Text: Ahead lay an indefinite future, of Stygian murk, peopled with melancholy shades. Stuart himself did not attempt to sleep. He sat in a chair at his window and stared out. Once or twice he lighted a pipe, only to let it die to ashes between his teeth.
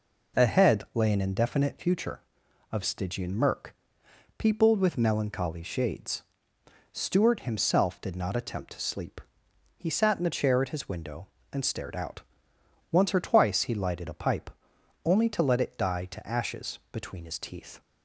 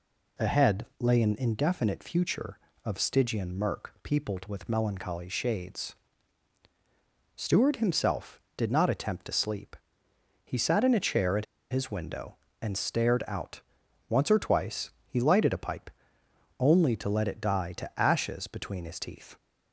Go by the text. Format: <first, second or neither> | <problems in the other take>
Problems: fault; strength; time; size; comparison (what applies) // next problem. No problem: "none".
first | pauses between "at" and "his"; slight; at 11.4 s; 0.27 s long // pauses between "twice" and "he"; slight; at 14.8 s; 0.18 s long